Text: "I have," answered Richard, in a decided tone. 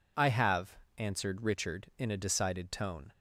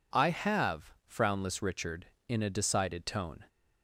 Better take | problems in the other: first | says "frownless" for "answered"; at 1.0 s

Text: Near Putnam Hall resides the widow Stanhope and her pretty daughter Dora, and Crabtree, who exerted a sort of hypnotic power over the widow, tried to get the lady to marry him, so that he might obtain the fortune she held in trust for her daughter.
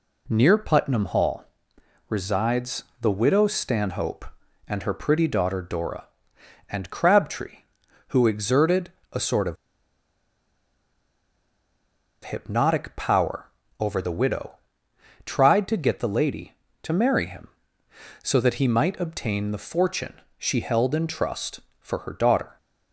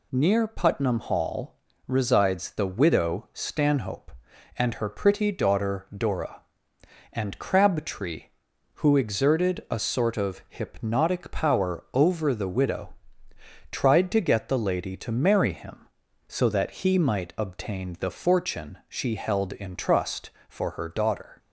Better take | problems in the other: second | pauses between "Hall" and "resides"; noticeable; at 1.4 s; 0.64 s long; slight in the second // pauses between "resides" and "the"; slight; at 2.8 s; 0.16 s long // pauses between "exerted" and "a"; slight; at 8.9 s; 0.22 s long // pauses between "of" and "hypnotic"; strong; at 9.5 s; 2.6 s long // pauses between "power" and "over"; slight; at 13.4 s; 0.32 s long // pauses between "fortune" and "she"; slight; at 20.1 s; 0.24 s long

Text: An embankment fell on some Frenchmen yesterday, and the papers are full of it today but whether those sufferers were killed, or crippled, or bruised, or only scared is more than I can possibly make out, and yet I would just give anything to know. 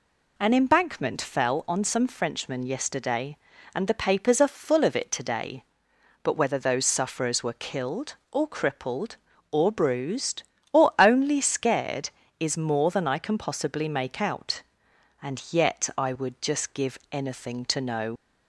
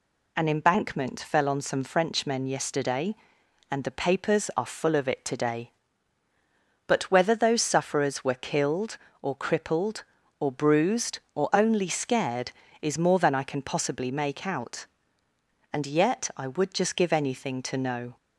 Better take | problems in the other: second | leaves "know" unfinished; at 18.1 s; 75 ms

